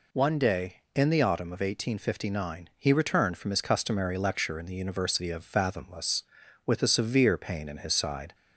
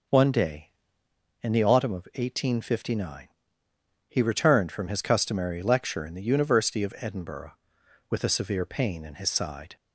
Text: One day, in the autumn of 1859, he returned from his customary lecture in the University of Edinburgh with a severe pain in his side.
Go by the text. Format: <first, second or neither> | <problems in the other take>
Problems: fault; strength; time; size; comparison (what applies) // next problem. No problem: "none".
second | says "Fathomless" for "Edinburgh"; at 5.4 s